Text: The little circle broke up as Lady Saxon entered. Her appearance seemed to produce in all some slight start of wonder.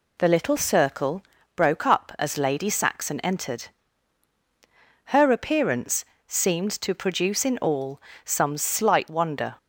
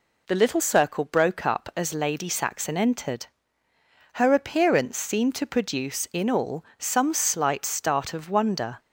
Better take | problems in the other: second | pauses between "circle" and "broke"; slight; at 1.2 s; 0.34 s long // pauses between "appearance" and "seemed"; slight; at 6.0 s; 0.22 s long // pauses between "all" and "some"; slight; at 8.0 s; 0.24 s long // skips "start of"; at 9.0 s

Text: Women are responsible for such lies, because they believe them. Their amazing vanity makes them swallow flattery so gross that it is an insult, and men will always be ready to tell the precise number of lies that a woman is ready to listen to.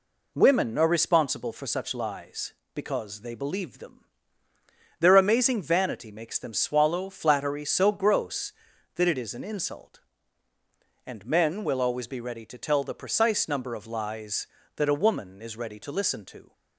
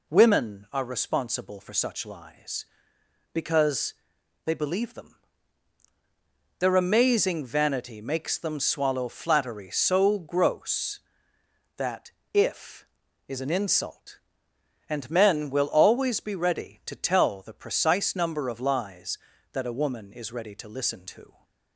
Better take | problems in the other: first | pauses between "because" and "they"; noticeable; at 3.9 s; 0.52 s long // says "if" for "it"; at 12.3 s

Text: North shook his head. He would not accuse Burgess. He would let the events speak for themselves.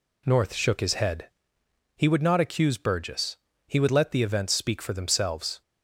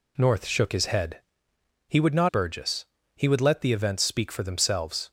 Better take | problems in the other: first | skips "accuse"; at 2.2 s

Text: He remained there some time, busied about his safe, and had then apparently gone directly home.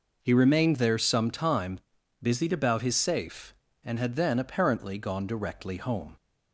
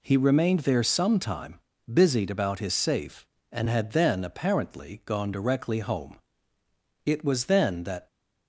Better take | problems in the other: first | goes on to say "It was then that"; noticeable; from 7.0 s on; 1.0 s long

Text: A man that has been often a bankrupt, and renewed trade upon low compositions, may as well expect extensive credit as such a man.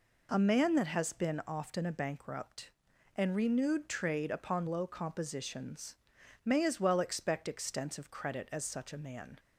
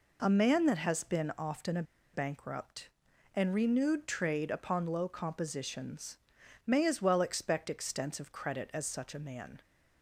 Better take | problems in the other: first | pauses between "a" and "bankrupt"; slight; at 1.8 s; 0.30 s long

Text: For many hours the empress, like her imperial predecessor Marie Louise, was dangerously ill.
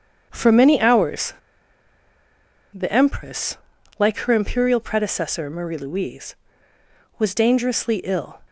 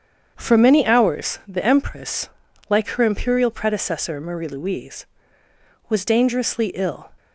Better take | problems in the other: second | starts louder than the rest; strong; until 1.3 s; 7.5 dB; strong in the second // pauses between "hours" and "the"; strong; at 1.3 s; 1.3 s long

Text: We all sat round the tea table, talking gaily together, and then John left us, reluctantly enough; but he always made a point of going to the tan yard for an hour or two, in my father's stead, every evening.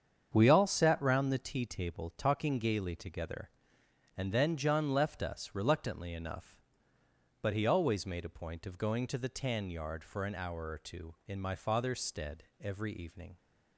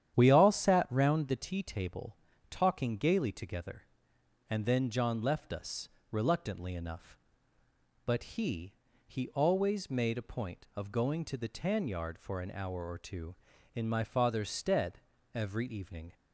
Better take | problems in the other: first | starts louder than the rest; strong; until 1.1 s; 10 dB; strong in the first // says "he" twice; at 9.0 s

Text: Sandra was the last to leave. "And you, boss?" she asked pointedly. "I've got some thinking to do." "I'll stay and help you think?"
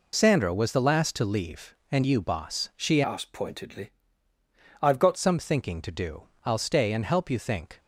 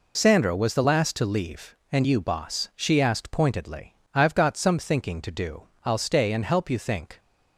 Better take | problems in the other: second | changes voice from "asked" to "got"; from 3.0 to 5.1 s; 2.1 s long

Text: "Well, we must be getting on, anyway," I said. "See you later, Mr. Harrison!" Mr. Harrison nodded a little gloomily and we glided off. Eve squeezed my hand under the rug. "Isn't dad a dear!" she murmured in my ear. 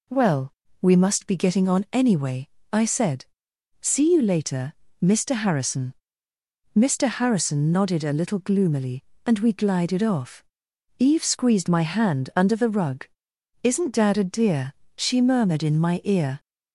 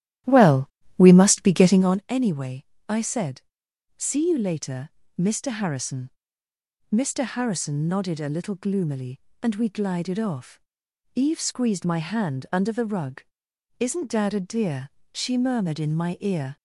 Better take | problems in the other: first | starts louder than the rest; strong; until 2.1 s; 12.5 dB

